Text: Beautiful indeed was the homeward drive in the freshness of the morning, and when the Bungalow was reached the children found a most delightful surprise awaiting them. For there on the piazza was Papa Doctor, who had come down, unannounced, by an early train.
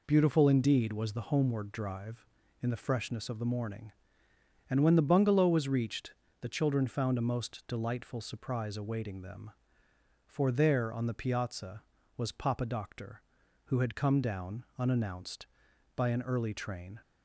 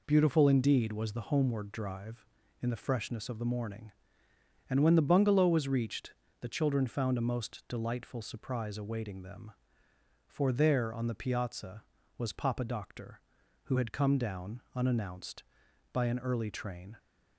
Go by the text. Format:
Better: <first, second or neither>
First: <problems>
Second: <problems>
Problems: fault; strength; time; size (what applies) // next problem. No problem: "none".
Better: neither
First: pauses between "reached" and "the"; slight; at 6.1 s; 0.30 s long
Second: pauses between "reached" and "the"; slight; at 6.1 s; 0.30 s long